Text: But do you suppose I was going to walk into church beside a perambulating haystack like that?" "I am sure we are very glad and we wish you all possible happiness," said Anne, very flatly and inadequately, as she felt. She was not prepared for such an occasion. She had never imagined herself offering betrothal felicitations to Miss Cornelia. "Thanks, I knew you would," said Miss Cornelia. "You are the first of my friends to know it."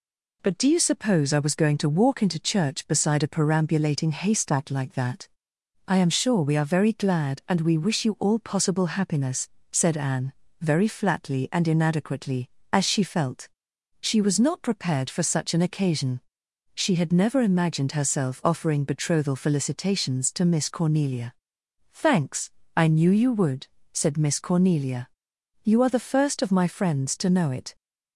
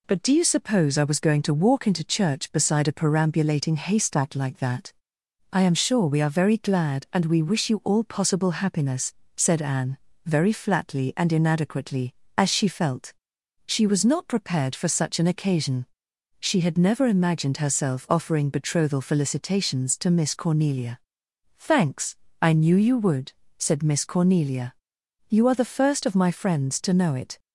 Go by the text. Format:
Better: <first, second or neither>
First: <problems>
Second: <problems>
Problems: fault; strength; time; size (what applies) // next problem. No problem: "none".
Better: neither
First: none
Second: none